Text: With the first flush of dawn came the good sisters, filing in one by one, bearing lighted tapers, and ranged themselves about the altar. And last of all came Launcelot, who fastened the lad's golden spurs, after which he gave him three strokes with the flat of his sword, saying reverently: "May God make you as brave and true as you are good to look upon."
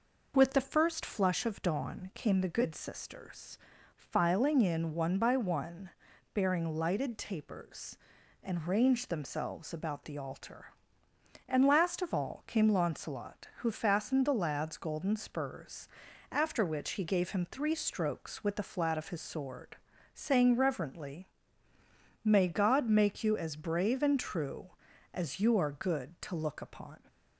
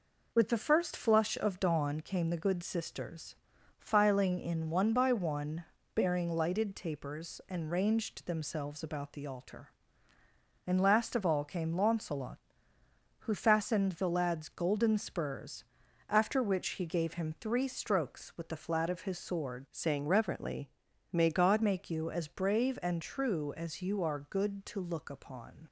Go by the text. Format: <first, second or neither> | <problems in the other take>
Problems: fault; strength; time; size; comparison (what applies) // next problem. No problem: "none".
first | changes voice from "saying" to "God"; from 19.7 to 21.6 s; 1.9 s long